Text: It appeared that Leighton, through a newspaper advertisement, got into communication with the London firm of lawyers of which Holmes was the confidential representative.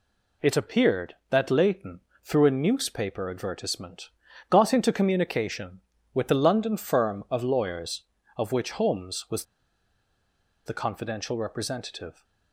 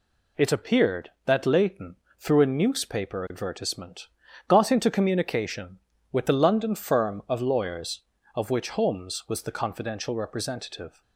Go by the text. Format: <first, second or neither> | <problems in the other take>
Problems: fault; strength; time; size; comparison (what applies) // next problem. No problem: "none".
second | pauses between "was" and "the"; at 9.4 s; 1.2 s long